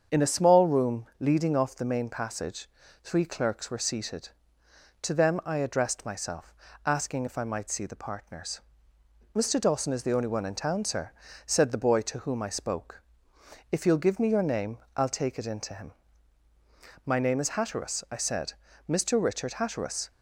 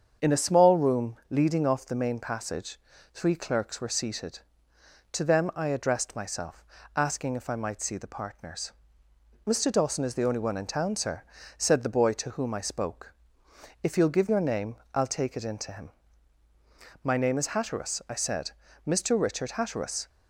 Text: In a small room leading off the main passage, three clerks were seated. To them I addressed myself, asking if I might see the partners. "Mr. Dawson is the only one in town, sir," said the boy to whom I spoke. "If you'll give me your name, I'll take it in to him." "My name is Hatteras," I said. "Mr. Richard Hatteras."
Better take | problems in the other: first | starts louder than the rest; strong; until 1.3 s; 7 dB; strong in the first // skips "me"; at 14.2 s

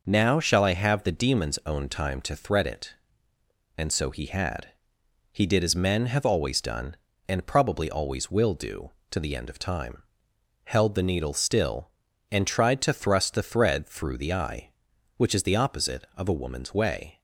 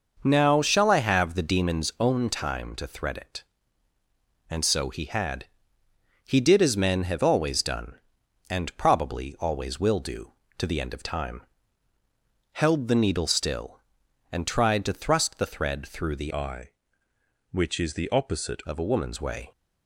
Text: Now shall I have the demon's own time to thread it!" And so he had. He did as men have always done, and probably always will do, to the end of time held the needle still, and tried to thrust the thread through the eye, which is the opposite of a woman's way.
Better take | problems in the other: first | pauses between "time" and "held"; at 11.4 s; 1.1 s long; noticeable in the first // changes voice from "eye" to "opposite"; from 16.3 to 18.6 s; 2.3 s long

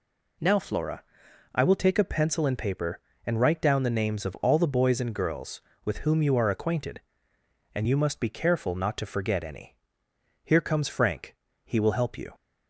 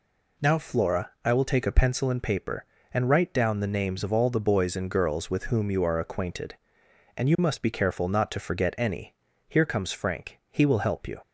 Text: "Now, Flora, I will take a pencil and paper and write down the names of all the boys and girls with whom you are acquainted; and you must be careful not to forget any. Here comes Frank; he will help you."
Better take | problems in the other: neither | none

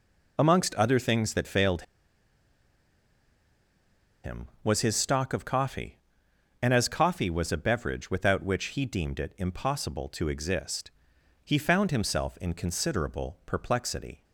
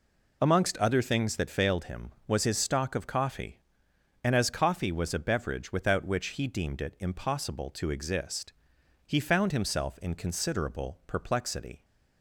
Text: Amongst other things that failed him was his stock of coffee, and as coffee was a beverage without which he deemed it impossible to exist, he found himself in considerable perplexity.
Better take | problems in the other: second | pauses between "failed" and "him"; strong; at 1.8 s; 2.4 s long

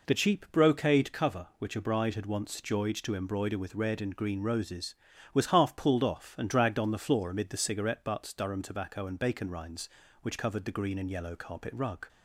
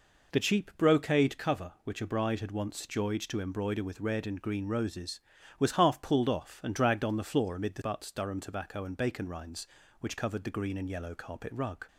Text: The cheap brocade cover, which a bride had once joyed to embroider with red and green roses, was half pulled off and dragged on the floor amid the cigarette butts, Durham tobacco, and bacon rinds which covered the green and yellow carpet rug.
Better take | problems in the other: first | skips "cigarette"; at 7.8 s

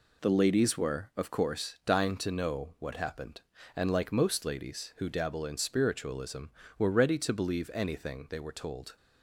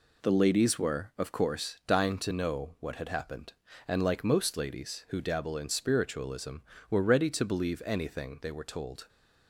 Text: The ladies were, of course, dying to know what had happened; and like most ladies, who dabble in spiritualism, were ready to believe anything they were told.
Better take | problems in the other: second | skips "had"; at 2.9 s

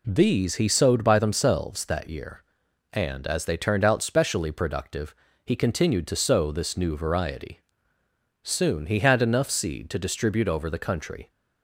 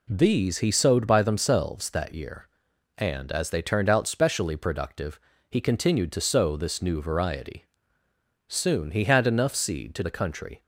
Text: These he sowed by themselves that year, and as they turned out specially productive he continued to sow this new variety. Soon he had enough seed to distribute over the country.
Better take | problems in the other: first | pauses between "productive" and "he"; slight; at 5.1 s; 0.32 s long; slight in the first // skips "distribute over"; at 10.0 s

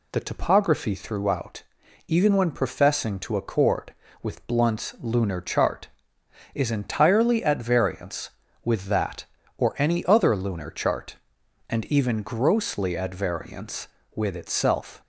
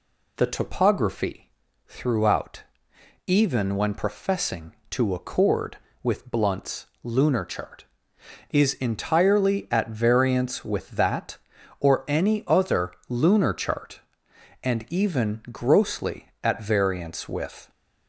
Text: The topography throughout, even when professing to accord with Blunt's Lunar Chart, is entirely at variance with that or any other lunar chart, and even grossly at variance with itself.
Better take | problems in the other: first | pauses between "topography" and "throughout"; at 1.4 s; 0.40 s long // pauses between "Blunt's" and "Lunar"; slight; at 6.8 s; 0.16 s long // pauses between "other" and "lunar"; slight; at 12.9 s; 0.16 s long // stops before "itself"; at 17.6 s

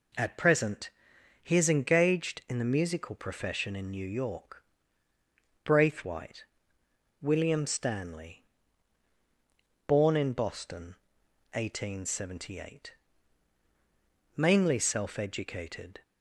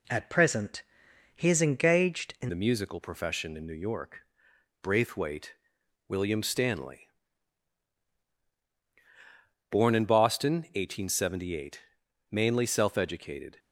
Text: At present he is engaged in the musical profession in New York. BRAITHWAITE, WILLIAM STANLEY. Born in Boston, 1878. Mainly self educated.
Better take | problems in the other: first | pauses between "present" and "he"; noticeable; at 0.8 s; 0.52 s long; noticeable in the first // changes voice at "the"; from 2.4 s on; 11.1 s long

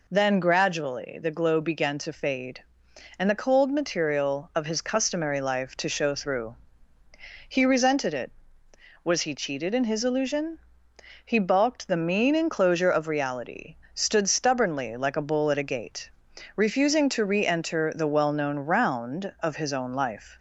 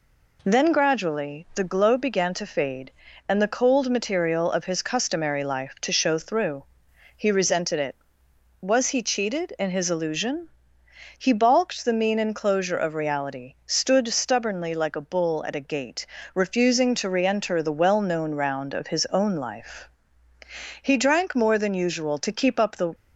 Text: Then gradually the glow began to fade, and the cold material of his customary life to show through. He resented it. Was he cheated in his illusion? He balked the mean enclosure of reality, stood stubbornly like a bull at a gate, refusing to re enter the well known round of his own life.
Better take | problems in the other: first | goes on to say "He drank more than usual to keep up the"; strong; from 20.8 s on; 2.1 s long

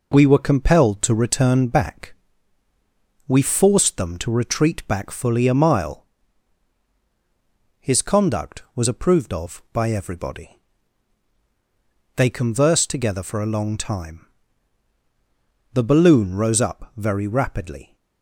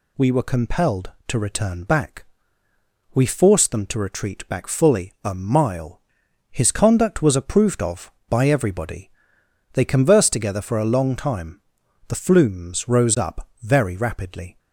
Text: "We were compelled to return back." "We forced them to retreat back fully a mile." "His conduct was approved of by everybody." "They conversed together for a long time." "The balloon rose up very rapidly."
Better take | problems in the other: first | says "flumes" for "balloon"; at 12.1 s

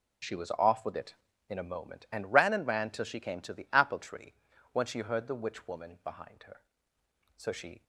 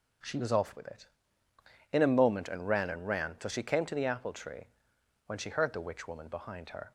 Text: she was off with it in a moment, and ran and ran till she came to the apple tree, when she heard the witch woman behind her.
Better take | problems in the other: second | goes on to say "So she"; slight; from 7.3 s on; 0.46 s long

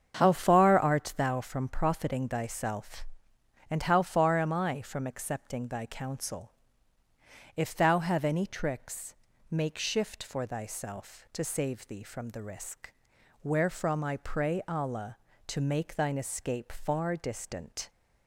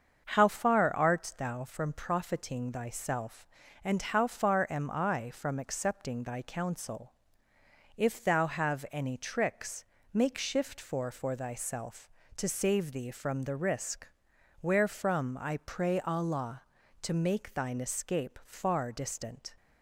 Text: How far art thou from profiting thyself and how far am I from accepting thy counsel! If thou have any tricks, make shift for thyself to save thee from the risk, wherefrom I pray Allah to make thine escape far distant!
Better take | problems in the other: first | starts louder than the rest; until 1.2 s; 6.5 dB; strong in the first // says "for" twice; at 11.1 s

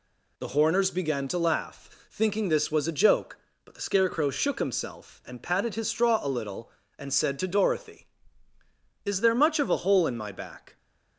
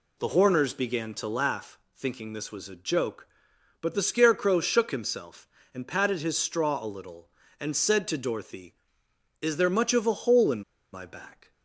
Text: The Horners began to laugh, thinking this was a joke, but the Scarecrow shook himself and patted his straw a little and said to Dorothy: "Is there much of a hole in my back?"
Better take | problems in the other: first | pauses between "in" and "my"; slight; at 10.6 s; 0.32 s long

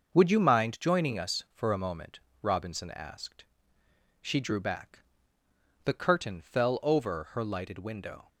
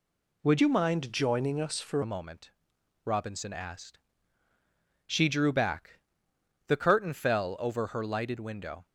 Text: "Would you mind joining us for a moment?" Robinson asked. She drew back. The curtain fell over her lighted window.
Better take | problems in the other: first | changes voice from "you" to "for"; from 0.6 to 2.0 s; 1.4 s long

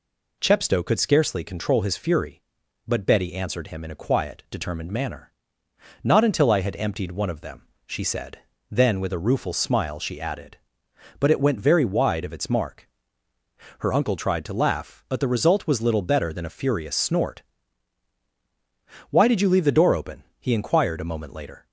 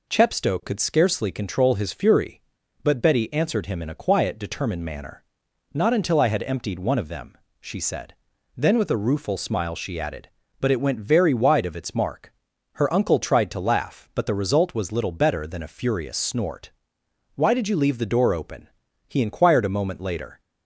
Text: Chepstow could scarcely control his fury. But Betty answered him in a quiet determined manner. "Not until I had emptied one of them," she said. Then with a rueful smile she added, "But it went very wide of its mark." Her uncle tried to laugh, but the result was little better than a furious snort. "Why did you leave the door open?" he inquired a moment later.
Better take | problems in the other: neither | none

